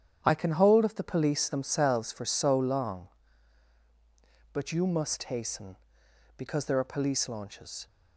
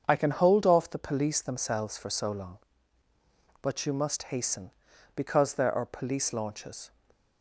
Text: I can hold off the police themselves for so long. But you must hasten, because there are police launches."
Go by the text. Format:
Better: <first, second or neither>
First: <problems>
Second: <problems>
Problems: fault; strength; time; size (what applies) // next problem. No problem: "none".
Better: second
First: starts louder than the rest; strong; until 1.2 s; 9 dB // says "of" for "off"; at 0.8 s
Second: starts louder than the rest; until 1.0 s; 7 dB